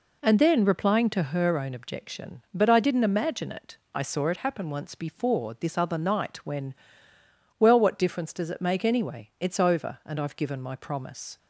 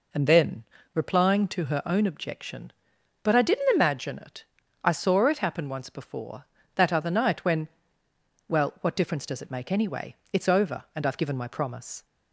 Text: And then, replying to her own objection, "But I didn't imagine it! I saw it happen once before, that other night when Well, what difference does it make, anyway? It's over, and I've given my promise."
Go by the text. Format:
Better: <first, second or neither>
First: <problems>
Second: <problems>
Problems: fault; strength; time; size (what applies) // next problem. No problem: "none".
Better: second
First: says "this" for "that"; at 5.5 s // pauses between "when" and "Well"; noticeable; at 6.7 s; 0.86 s long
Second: pauses between "when" and "Well"; noticeable; at 7.6 s; 0.82 s long